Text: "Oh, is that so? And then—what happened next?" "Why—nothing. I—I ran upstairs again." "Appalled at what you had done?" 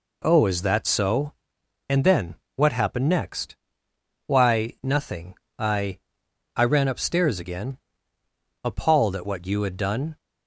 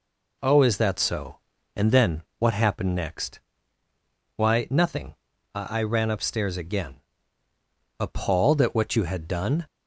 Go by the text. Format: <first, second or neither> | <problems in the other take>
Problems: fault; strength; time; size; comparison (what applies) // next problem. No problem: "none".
neither | none